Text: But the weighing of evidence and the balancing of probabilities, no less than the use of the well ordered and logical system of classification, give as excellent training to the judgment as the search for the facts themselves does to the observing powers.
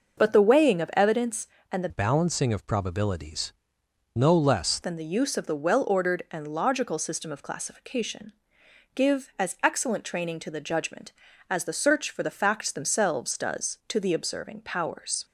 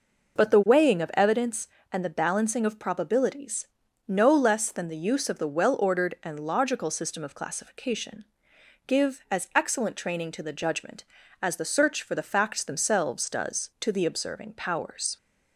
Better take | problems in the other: second | changes voice from "balancing" to "less"; from 1.8 to 4.7 s; 2.9 s long

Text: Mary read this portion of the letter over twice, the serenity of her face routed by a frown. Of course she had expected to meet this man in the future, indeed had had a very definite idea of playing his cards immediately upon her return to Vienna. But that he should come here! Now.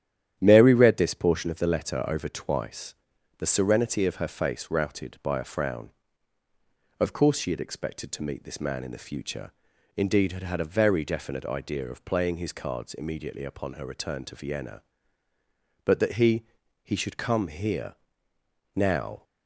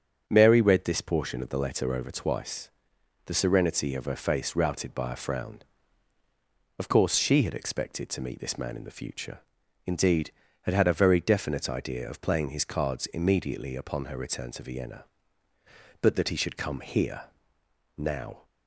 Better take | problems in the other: second | starts louder than the rest; strong; until 1.4 s; 10.5 dB; also in the second // says "he" twice; at 16.8 s

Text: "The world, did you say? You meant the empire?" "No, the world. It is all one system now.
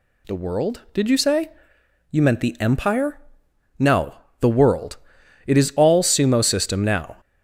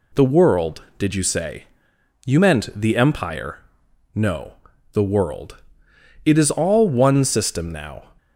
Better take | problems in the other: second | says "sumo" for "one"; at 6.0 s

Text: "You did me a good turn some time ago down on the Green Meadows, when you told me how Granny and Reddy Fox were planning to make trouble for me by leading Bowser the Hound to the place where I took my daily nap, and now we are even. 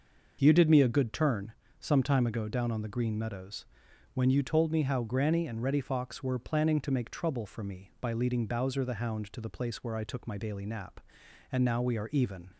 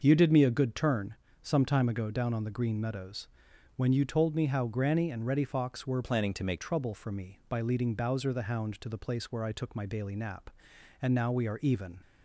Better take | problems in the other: first | starts louder than the rest; noticeable; until 1.0 s; 6 dB; noticeable in the first // pauses between "turn" and "some"; slight; at 1.1 s; 0.30 s long; slight in the first // changes voice from "planning" to "make"; from 6.0 to 6.6 s; 0.6 s long

